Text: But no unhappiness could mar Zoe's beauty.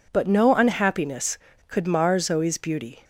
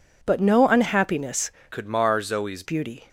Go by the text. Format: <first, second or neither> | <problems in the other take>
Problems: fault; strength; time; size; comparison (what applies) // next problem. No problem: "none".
first | changes voice from "could" to "Zoe's"; from 1.7 to 2.6 s; 0.9 s long